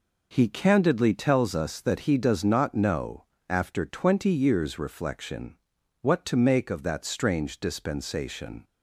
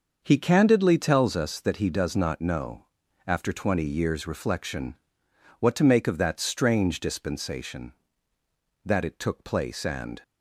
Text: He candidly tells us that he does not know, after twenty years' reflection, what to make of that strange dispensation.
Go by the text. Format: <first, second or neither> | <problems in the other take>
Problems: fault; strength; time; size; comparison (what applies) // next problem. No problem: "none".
first | starts louder than the rest; until 1.2 s; 6.5 dB // goes on to say "That it took place and"; from 8.8 s on; 1.3 s long